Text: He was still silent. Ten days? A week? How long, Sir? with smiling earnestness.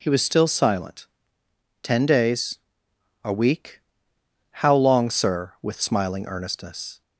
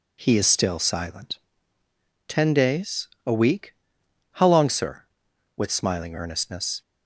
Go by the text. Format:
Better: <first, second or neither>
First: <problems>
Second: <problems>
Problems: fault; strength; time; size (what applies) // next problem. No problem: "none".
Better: first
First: none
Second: says "is" for "was"; at 0.3 s